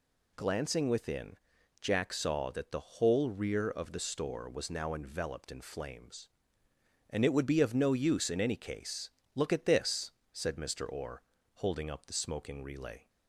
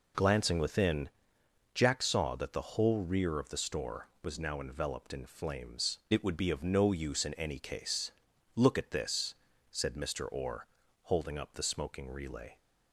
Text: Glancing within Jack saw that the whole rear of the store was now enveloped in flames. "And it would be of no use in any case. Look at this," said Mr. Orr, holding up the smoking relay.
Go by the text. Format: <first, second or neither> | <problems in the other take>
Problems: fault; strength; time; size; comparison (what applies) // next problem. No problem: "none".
first | pauses between "within" and "Jack"; noticeable; at 1.0 s; 0.64 s long; also in the first // skips "And"; at 6.0 s